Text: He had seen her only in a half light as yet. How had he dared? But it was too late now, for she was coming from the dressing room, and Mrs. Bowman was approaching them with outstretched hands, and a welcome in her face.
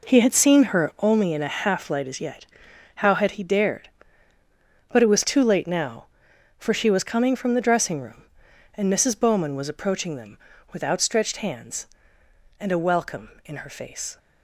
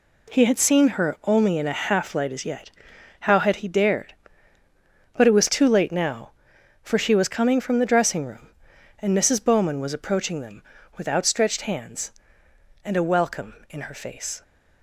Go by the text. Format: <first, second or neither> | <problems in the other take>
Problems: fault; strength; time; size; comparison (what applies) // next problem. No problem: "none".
second | starts louder than the rest; noticeable; until 1.2 s; 4 dB